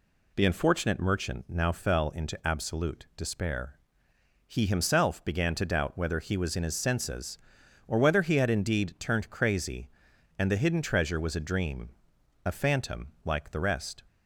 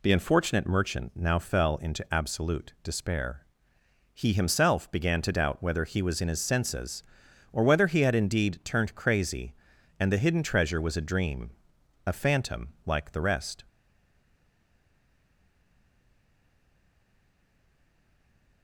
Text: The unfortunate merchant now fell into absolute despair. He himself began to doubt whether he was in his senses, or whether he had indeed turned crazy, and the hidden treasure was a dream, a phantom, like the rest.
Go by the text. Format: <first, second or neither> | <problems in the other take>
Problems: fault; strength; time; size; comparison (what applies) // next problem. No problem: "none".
first | stays silent after the last word; strong; from 13.6 s on; 5.0 s long